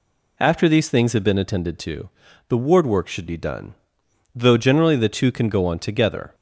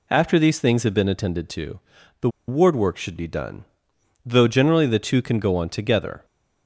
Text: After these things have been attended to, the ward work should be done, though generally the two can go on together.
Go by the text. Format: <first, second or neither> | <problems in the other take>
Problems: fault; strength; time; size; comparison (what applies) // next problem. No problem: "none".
first | pauses between "the" and "ward"; slight; at 2.2 s; 0.18 s long